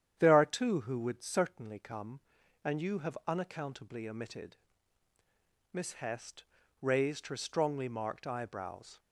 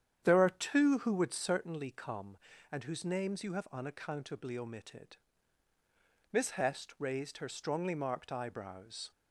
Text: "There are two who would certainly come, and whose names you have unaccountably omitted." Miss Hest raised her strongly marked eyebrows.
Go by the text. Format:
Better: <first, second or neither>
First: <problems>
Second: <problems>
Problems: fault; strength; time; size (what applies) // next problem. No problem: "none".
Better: second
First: starts louder than the rest; strong; until 1.2 s; 9.5 dB // skips "whose names"; at 2.8 s // pauses between "Hest" and "raised"; at 6.4 s; 0.38 s long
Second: starts louder than the rest; strong; until 1.2 s; 9 dB